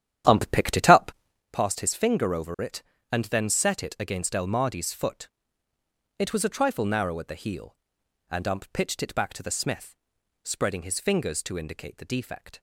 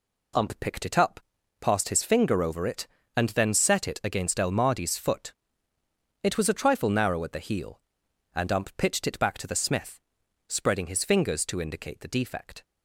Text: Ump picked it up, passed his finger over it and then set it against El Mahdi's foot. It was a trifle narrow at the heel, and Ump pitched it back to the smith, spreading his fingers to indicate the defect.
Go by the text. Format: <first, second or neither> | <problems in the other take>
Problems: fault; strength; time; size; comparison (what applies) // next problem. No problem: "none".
second | starts louder than the rest; strong; until 1.5 s; 10.5 dB